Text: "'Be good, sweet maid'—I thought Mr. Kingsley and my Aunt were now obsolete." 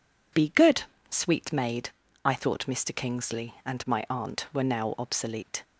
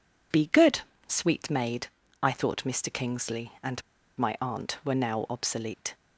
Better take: first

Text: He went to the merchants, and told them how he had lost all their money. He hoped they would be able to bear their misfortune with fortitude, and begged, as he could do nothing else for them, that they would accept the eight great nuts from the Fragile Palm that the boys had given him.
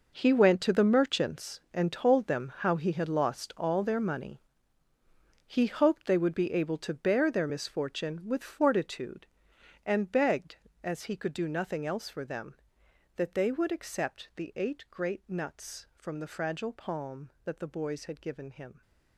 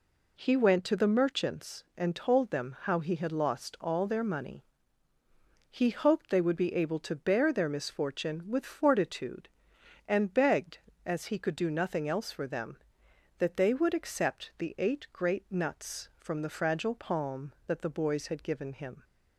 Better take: second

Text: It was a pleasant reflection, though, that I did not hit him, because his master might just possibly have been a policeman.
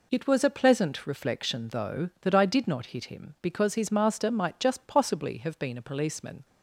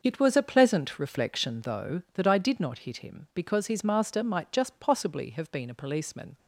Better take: first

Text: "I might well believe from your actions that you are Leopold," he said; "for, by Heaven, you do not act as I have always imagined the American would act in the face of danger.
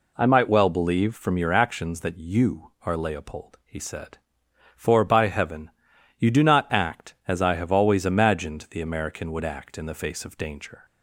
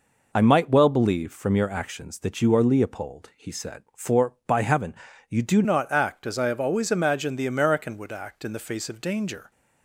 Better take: first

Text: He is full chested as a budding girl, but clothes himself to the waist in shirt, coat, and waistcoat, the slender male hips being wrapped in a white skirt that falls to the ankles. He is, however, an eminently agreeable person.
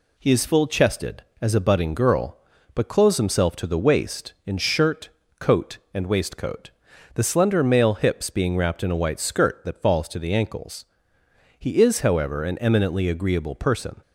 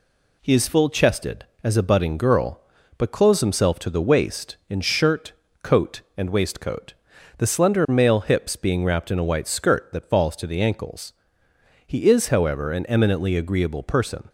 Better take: neither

